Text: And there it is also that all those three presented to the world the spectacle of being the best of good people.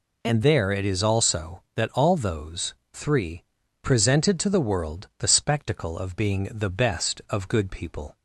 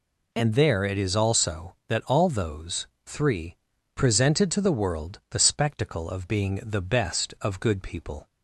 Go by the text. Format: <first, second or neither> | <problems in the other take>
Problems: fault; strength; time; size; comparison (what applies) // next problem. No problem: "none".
neither | pauses between "those" and "three"; slight; the same in both // pauses between "three" and "presented"; the same in both